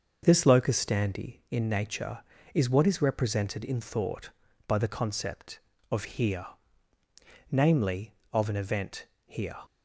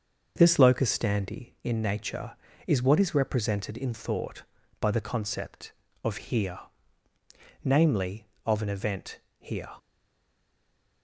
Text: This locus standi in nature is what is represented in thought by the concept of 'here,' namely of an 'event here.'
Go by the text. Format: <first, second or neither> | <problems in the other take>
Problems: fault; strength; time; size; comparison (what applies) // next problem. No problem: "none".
first | starts louder than the rest; until 1.3 s; 6.5 dB; also in the first // pauses between "event" and "here"; slight; at 9.1 s; 0.22 s long; slight in the first // stays silent after the last word; noticeable; from 9.7 s on; 1.3 s long